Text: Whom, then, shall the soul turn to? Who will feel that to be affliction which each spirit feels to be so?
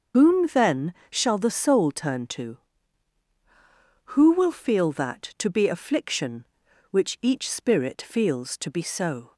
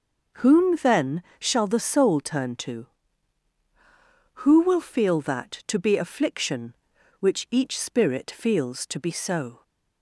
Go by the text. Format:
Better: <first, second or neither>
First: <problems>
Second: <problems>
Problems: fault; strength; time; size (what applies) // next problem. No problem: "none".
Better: second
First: loses the start of "Whom"; at 0.1 s; 80 ms // starts louder than the rest; noticeable; until 1.3 s; 6 dB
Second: none